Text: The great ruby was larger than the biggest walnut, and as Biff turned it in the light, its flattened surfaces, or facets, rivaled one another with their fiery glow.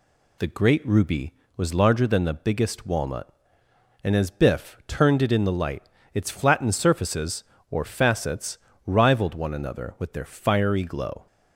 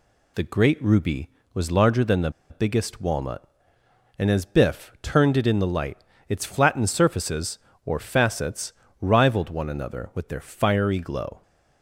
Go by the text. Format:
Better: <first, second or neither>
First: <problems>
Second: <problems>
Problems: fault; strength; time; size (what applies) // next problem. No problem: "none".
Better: first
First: none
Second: pauses between "the" and "biggest"; slight; at 2.3 s; 0.19 s long